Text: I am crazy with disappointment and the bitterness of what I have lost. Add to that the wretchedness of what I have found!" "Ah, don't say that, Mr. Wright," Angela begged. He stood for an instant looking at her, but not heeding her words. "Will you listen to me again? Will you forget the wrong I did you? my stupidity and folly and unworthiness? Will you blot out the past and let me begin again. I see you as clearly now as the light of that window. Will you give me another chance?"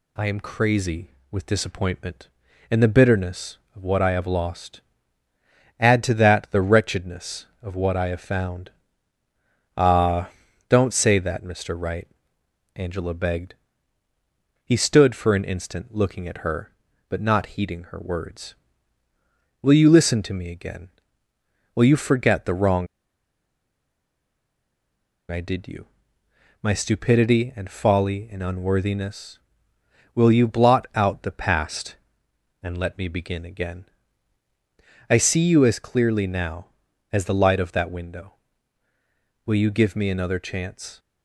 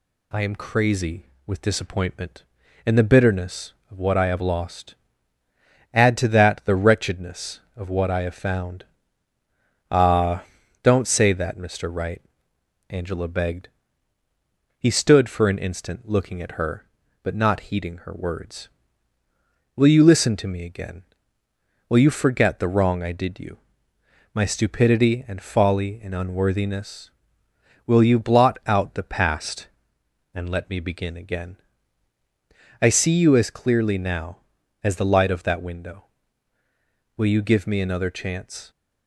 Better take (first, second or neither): second